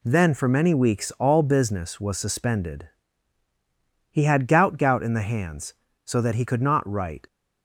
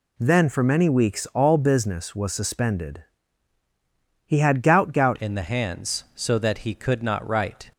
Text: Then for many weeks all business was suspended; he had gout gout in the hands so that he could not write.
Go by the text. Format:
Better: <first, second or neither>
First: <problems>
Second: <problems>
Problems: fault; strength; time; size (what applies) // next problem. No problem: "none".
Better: first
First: none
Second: changes voice at "in"; from 5.1 s on; 2.6 s long